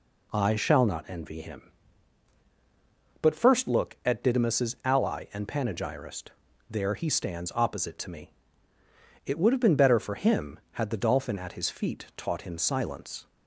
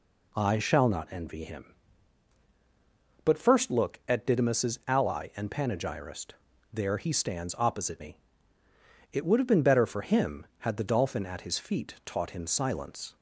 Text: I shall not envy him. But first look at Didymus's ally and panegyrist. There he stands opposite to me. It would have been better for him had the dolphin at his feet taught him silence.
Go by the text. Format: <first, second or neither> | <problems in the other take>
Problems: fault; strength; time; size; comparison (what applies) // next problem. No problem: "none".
first | skips "to"; at 7.9 s